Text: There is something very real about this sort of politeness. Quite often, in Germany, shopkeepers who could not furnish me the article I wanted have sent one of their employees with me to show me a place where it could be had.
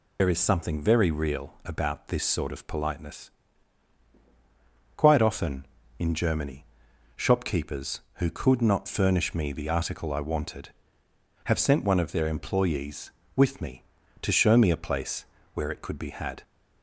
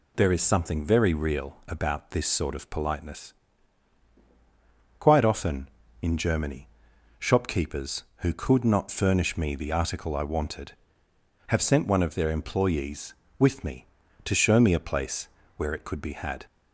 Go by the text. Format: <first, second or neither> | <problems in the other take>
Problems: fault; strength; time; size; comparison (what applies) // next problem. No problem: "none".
second | loses the start of "There"; at 0.1 s; 75 ms // pauses between "place" and "where"; slight; at 15.2 s; 0.30 s long; slight in the second